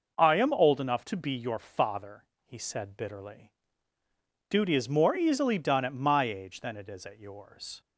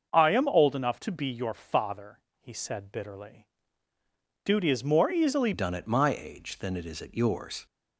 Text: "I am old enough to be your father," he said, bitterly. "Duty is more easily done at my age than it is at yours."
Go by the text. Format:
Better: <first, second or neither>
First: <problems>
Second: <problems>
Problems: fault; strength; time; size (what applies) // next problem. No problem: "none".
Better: first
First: none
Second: starts louder than the rest; until 1.1 s; 6 dB // changes voice at "done"; from 5.5 s on; 2.1 s long